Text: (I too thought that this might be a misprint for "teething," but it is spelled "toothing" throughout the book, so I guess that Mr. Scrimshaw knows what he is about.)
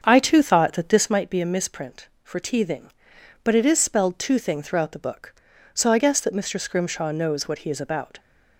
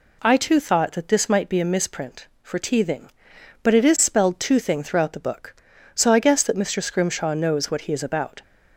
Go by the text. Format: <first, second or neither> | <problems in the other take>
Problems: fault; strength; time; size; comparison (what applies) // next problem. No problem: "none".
second | starts louder than the rest; until 1.1 s; 7 dB